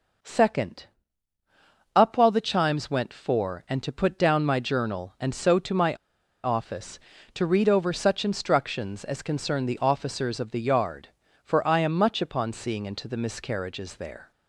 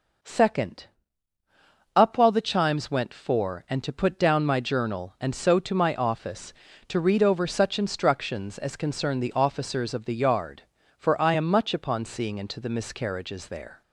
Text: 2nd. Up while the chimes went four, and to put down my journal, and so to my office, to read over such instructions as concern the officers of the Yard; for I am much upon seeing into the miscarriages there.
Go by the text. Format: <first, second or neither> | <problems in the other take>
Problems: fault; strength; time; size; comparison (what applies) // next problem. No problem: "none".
second | pauses between "my" and "office"; noticeable; at 5.9 s; 0.49 s long